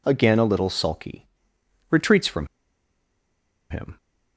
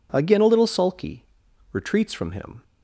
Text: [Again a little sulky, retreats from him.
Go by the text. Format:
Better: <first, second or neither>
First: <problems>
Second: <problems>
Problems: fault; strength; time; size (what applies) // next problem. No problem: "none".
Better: second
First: pauses between "from" and "him"; at 2.4 s; 1.2 s long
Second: none